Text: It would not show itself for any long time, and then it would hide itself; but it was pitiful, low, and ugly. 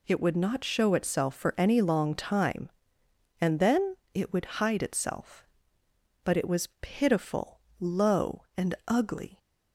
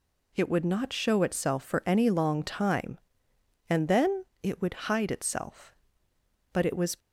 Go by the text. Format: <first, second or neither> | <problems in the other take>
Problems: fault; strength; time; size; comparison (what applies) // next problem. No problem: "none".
first | pauses between "then" and "it"; slight; at 4.2 s; 0.18 s long; slight in the first // stops before "pitiful low and ugly"; at 6.9 s